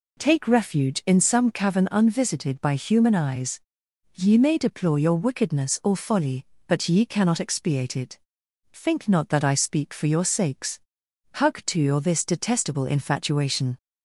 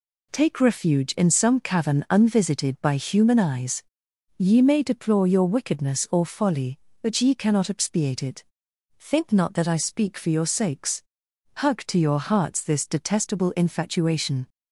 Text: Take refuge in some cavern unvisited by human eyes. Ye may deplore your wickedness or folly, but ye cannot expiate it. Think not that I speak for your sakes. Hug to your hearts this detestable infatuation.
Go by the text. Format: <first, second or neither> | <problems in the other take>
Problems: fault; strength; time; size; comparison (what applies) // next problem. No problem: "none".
second | skips "hearts"; at 12.0 s